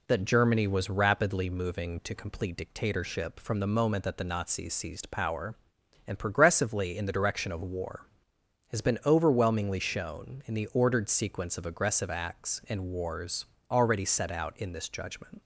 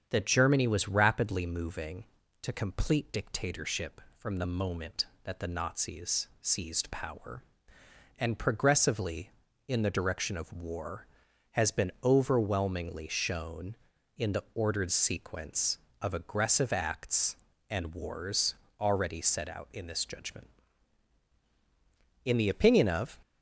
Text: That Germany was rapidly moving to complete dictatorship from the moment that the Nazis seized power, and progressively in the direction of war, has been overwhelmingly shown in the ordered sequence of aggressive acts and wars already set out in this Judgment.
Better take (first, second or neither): first